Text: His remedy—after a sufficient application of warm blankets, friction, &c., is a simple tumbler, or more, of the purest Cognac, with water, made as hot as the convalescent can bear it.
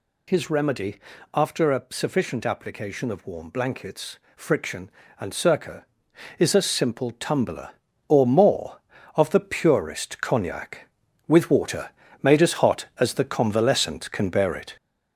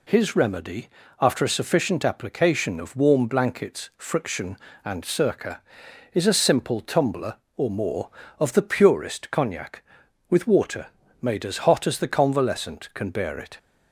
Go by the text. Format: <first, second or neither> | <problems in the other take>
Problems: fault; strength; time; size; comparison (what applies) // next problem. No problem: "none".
second | gets louder; noticeable; throughout; 5.5 dB